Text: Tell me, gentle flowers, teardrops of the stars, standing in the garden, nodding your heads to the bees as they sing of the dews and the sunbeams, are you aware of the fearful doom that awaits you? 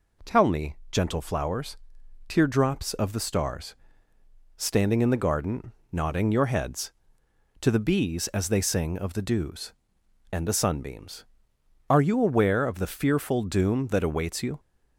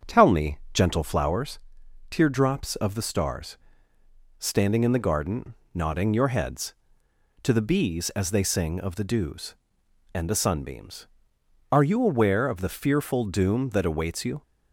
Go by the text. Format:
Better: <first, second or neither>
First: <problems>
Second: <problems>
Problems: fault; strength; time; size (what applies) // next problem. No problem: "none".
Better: first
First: none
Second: starts louder than the rest; strong; until 1.6 s; 7.5 dB